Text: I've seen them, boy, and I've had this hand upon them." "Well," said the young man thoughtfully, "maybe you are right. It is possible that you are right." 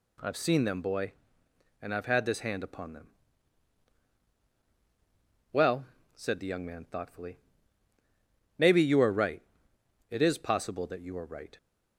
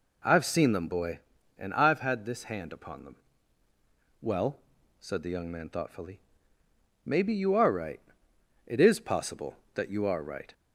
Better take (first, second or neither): neither